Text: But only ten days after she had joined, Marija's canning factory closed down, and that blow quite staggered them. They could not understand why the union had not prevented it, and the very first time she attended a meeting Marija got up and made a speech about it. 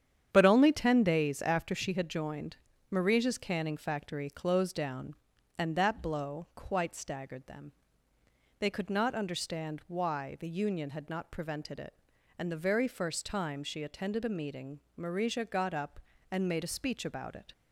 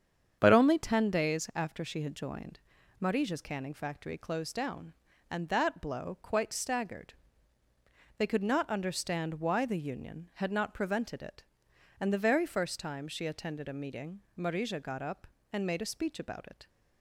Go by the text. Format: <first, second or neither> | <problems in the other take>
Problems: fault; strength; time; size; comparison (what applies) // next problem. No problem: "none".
first | starts louder than the rest; strong; until 1.4 s; 8 dB; strong in the first // skips "them"; at 7.6 s // pauses between "meeting" and "Marija"; slight; at 14.2 s; 0.16 s long; slight in the first